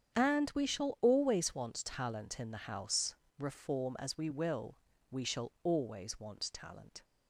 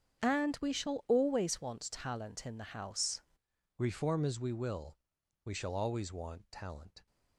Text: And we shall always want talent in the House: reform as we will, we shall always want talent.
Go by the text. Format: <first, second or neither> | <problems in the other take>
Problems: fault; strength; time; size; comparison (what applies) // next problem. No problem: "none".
first | starts louder than the rest; strong; until 1.2 s; 8 dB; strong in the first // changes voice at "reform"; from 3.7 s on; 3.3 s long